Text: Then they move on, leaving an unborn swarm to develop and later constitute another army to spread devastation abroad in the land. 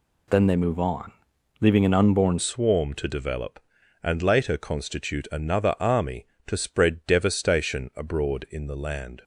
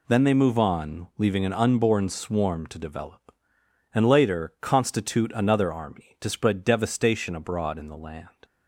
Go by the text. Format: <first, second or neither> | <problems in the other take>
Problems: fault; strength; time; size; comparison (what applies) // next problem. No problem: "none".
second | changes voice at "swarm"; from 2.3 s on; 6.9 s long